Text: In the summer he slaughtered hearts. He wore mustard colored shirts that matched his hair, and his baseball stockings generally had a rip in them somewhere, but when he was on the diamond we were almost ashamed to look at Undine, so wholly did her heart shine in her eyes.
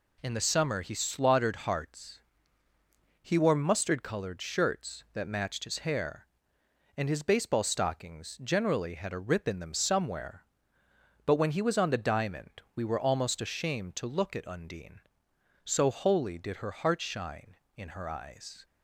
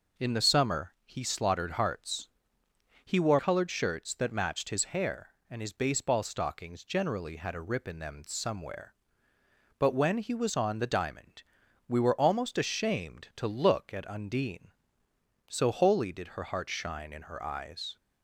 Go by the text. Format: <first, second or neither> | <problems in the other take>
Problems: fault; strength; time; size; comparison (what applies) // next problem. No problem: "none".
first | skips "mustard"; at 3.3 s // pauses between "diamond" and "we"; noticeable; at 11.4 s; 0.46 s long